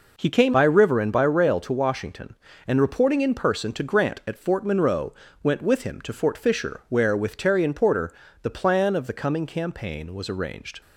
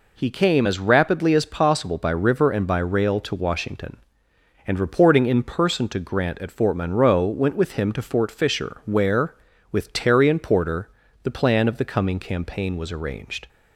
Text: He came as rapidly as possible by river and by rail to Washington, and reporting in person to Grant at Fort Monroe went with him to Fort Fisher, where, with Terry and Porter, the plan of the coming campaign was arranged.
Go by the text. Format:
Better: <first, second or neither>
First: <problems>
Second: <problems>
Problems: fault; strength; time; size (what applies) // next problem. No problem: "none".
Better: second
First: skips "as rapidly as possible"; at 0.5 s // pauses between "Monroe" and "went"; slight; at 5.1 s; 0.28 s long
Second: none